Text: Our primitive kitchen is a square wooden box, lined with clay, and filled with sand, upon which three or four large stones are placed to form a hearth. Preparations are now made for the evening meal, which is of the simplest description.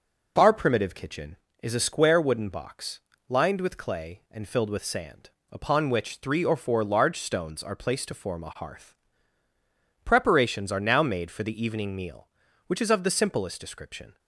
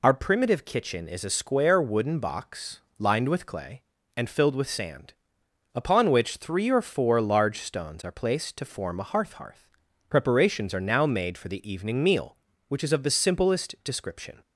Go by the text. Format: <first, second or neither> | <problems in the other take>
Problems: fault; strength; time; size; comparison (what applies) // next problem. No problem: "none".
first | says "hearth" twice; at 9.3 s